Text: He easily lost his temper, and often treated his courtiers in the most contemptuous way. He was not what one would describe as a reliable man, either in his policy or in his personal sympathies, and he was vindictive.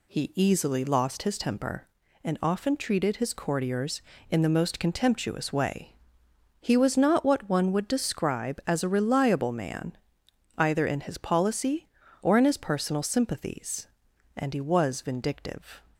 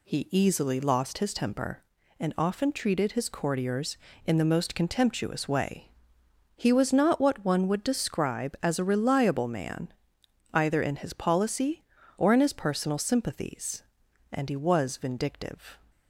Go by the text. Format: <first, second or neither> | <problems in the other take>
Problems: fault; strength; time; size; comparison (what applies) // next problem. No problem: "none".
neither | none